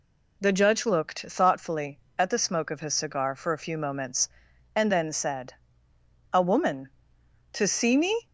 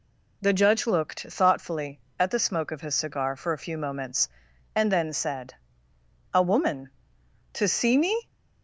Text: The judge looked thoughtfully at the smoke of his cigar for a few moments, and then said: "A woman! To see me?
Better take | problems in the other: neither | none

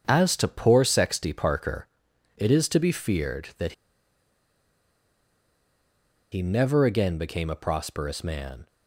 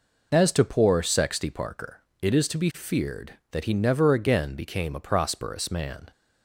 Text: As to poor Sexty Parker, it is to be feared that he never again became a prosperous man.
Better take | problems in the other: second | starts louder than the rest; strong; until 1.0 s; 7.5 dB // pauses between "that" and "he"; strong; at 3.7 s; 2.6 s long

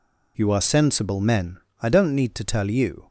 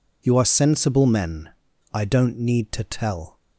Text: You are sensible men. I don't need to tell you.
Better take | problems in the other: first | stops before "you"; at 3.3 s

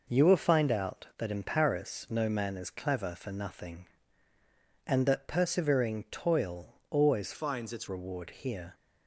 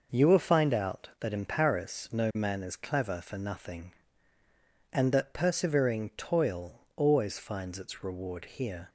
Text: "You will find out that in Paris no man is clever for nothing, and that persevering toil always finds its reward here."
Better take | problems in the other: second | changes voice from "finds" to "its"; from 7.3 to 7.8 s; 0.5 s long

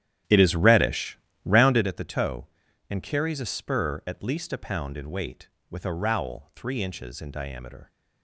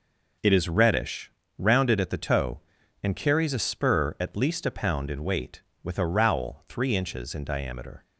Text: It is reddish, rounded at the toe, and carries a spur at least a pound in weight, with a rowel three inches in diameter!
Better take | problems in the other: second | starts louder than the rest; strong; until 1.9 s; 11 dB

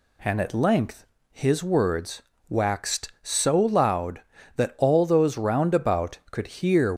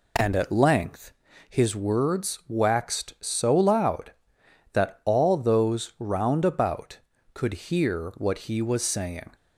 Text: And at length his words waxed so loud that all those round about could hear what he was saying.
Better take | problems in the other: second | pauses between "length" and "his"; slight; at 1.0 s; 0.28 s long; slight in the second // pauses between "words" and "waxed"; slight; at 2.2 s; 0.26 s long // stops before "what he was saying"; at 6.9 s

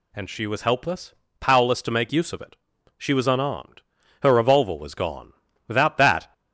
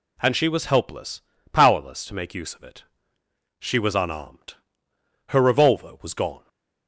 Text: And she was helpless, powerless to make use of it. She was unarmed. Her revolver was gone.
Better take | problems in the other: second | goes on to say "Without that"; noticeable; from 5.6 s on; 0.66 s long

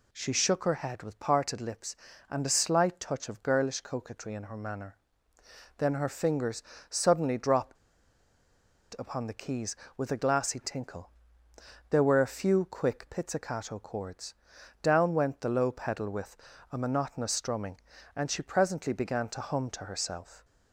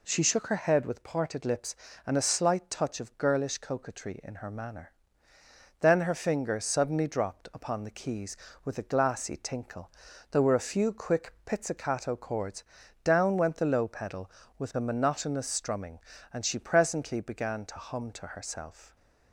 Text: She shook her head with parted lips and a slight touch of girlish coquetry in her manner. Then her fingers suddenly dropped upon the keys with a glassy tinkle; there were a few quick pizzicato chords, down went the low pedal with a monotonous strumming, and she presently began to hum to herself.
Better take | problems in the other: second | pauses between "fingers" and "suddenly"; slight; at 6.6 s; 0.26 s long // pauses between "dropped" and "upon"; at 7.7 s; 1.2 s long // pauses between "with" and "a"; slight; at 16.3 s; 0.34 s long

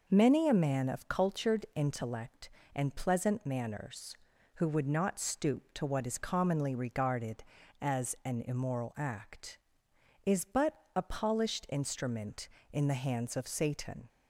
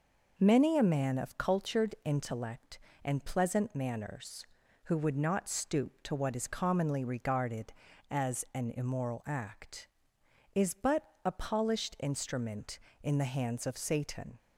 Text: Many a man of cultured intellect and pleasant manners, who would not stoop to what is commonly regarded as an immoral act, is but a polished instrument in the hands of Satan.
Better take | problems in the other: neither | pauses between "but" and "a"; slight; the same in both

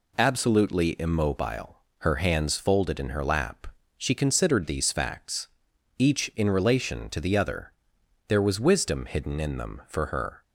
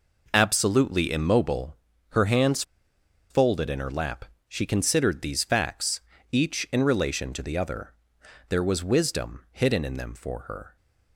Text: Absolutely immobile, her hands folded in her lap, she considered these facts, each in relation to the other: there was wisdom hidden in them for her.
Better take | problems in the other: first | pauses between "hands" and "folded"; noticeable; at 2.6 s; 0.67 s long

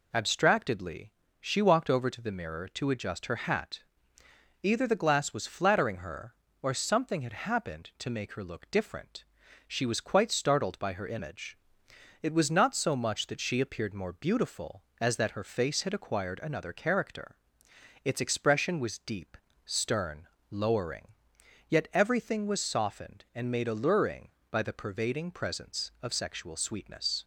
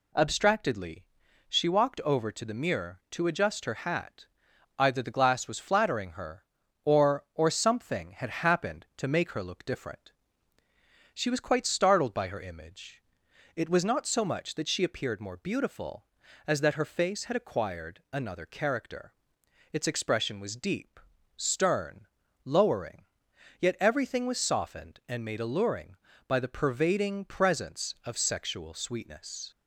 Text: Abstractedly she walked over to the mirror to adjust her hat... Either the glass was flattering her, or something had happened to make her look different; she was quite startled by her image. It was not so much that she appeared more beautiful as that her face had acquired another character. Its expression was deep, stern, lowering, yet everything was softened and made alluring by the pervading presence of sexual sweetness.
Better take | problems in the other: first | pauses between "Abstractedly" and "she"; at 1.0 s; 0.44 s long; slight in the first // says "or" twice; at 7.3 s

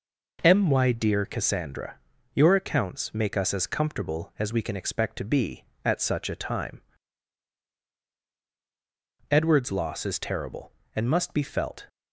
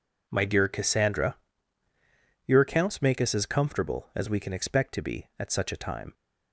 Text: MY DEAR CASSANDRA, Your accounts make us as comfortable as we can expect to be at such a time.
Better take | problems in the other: second | goes on to say "Edward's loss is terrible and must be felt"; strong; from 9.2 s on; 2.5 s long

